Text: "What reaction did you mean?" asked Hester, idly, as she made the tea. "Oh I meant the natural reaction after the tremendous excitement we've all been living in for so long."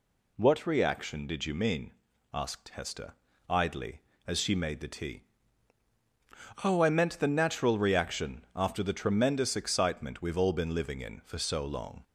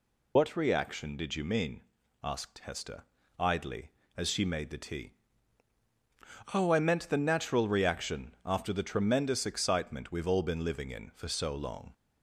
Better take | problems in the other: first | loses the start of "What"; at 0.3 s; 85 ms

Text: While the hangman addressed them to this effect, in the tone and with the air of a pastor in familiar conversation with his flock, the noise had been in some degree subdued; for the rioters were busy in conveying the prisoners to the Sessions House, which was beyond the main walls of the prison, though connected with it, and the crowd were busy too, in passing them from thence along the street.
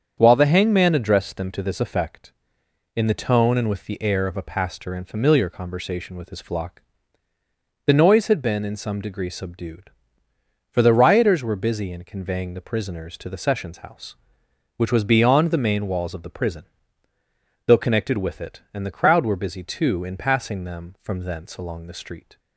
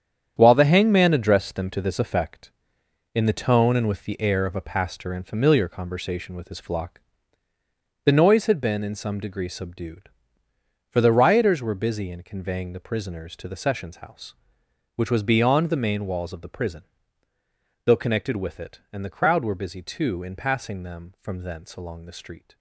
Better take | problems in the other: first | gets quieter; strong; throughout; 10.5 dB // starts louder than the rest; strong; until 1.3 s; 9 dB; strong in the first

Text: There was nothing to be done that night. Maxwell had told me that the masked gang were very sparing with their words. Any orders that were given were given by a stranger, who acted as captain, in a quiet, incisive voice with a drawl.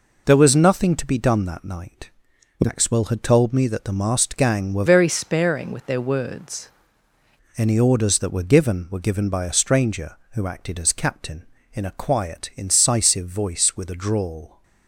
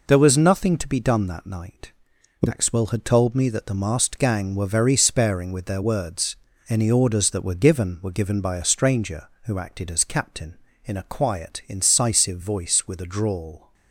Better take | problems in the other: second | changes voice from "very" to "words"; from 4.8 to 6.6 s; 1.8 s long

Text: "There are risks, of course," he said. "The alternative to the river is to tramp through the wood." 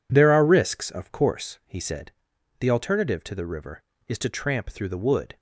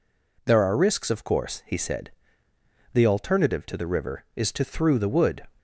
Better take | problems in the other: first | skips "tramp"; at 4.6 s

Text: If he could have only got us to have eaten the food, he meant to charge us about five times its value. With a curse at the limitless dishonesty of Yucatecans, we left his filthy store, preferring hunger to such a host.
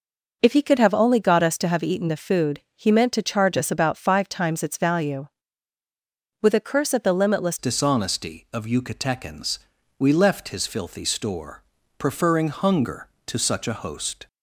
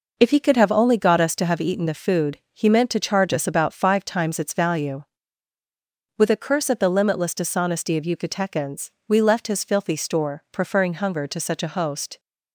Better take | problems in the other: second | changes voice at "dishonesty"; from 7.5 s on; 6.7 s long

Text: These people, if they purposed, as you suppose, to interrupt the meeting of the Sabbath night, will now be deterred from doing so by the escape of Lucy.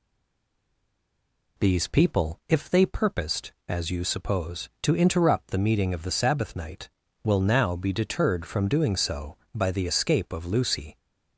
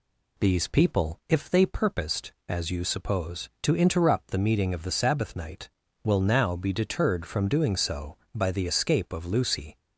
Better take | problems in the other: second | stays silent before the first word; noticeable; until 1.5 s; 1.5 s long

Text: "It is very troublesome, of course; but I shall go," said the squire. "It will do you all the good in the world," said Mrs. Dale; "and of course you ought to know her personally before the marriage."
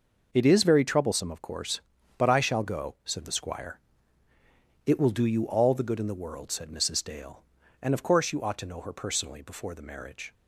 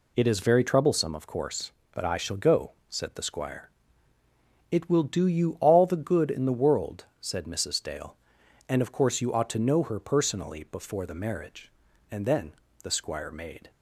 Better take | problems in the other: first | goes on to say "And then the squire made"; from 12.1 s on; 1.5 s long

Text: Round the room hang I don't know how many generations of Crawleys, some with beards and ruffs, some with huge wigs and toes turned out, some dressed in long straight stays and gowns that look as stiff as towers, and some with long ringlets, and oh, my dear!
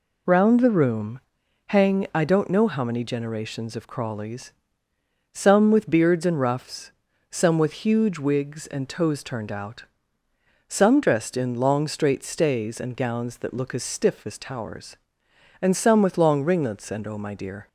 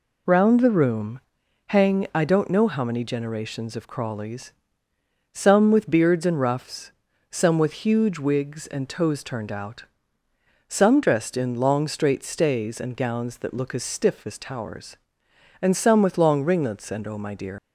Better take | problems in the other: first | pauses between "room" and "hang"; noticeable; at 1.1 s; 0.48 s long; noticeable in the first // leaves "dear" unfinished; at 17.5 s; 90 ms

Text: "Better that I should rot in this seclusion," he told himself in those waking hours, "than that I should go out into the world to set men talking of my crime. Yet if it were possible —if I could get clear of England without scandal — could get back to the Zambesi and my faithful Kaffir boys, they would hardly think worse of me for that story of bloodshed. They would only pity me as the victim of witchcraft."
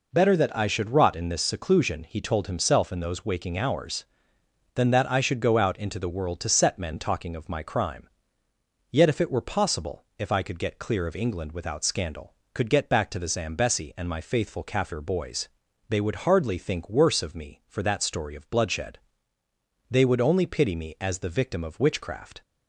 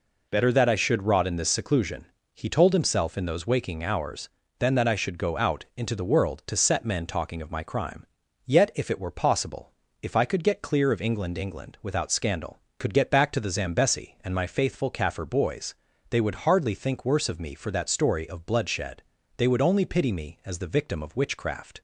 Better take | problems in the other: first | says "England" twice; at 11.3 s

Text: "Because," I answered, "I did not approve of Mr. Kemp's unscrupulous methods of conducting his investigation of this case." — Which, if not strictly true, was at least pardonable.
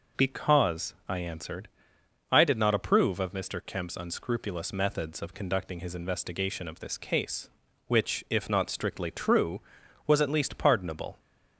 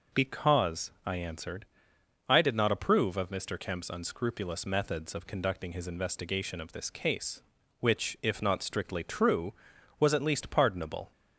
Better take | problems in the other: neither | none

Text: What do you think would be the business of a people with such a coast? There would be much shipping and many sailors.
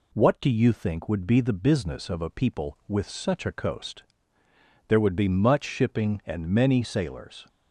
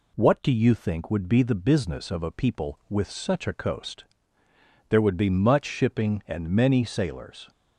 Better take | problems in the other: neither | none

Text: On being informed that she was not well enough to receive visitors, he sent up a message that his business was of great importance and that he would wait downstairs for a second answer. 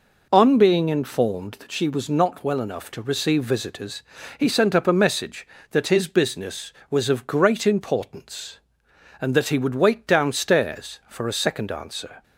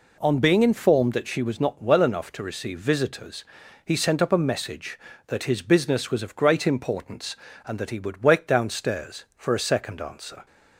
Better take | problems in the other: neither | none

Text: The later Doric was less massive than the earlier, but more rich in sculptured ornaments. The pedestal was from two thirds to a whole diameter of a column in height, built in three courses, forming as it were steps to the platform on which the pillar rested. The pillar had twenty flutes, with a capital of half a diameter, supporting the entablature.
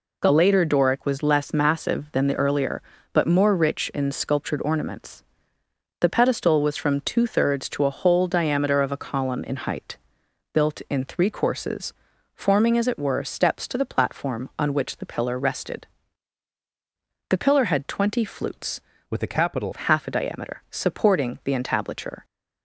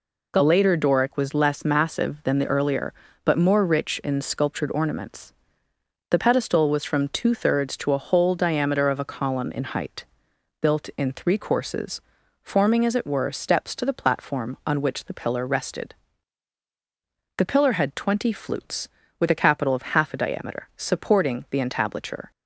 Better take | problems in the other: second | changes voice from "with" to "capital"; from 19.0 to 19.7 s; 0.7 s long

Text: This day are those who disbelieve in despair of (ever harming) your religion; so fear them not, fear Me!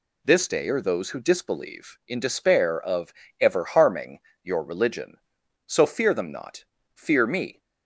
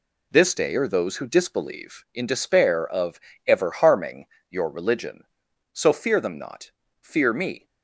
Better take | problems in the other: first | gets quieter; strong; throughout; 7.5 dB

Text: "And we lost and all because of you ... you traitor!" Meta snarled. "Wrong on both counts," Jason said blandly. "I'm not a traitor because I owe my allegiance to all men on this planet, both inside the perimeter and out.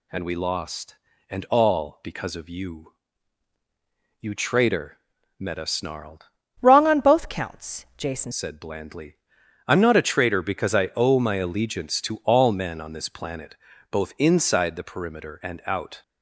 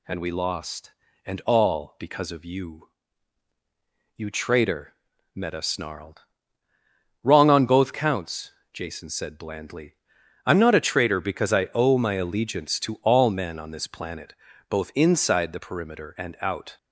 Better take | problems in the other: second | changes voice from "Wrong" to "Jason"; from 6.6 to 8.3 s; 1.7 s long

